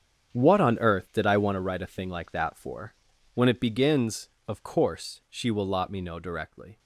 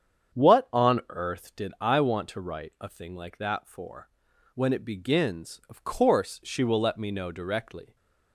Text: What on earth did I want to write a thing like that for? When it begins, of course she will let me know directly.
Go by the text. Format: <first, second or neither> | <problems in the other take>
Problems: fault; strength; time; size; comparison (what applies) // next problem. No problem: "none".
second | starts louder than the rest; strong; until 1.3 s; 8 dB; strong in the second // says "lot" for "let"; at 5.6 s